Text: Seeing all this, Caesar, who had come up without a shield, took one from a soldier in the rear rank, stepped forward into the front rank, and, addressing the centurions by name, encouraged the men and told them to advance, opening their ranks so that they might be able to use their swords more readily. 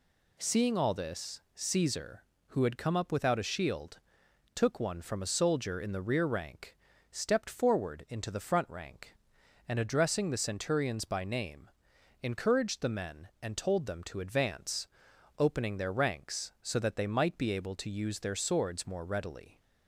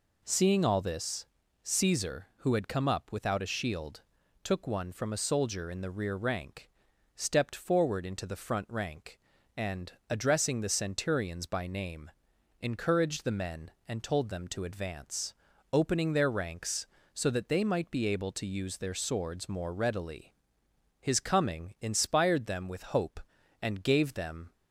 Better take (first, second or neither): first